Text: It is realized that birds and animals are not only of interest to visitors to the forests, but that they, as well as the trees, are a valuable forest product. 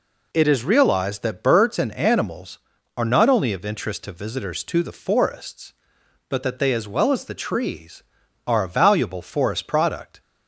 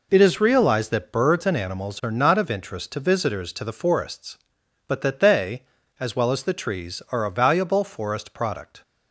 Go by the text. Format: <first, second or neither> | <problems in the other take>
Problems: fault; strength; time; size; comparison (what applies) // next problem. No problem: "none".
first | skips "only"; at 2.3 s